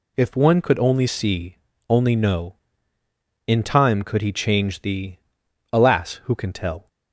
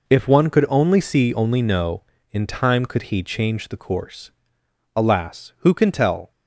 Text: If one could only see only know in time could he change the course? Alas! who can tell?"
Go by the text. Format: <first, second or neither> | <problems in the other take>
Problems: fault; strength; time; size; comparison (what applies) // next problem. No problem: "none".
second | pauses between "see" and "only"; slight; at 1.5 s; 0.34 s long // skips "course"; at 5.4 s